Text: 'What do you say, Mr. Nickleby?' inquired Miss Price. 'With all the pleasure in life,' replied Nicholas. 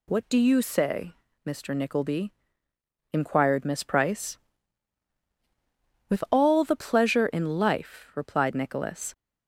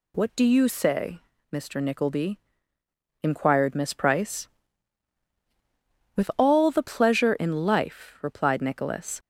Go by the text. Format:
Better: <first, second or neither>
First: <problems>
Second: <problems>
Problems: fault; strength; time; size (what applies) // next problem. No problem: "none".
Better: neither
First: none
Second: none